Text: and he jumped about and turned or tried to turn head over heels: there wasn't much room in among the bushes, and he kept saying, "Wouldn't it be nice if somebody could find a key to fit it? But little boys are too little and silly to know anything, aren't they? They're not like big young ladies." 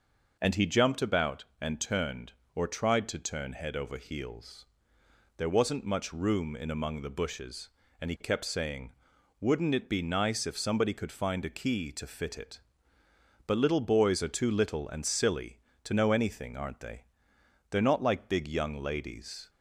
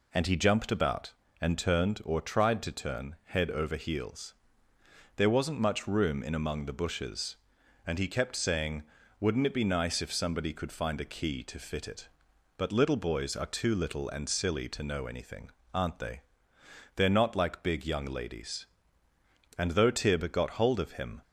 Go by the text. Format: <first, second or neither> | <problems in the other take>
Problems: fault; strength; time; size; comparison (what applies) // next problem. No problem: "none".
first | goes on to say "And though Tib got hold of him"; from 19.5 s on; 1.6 s long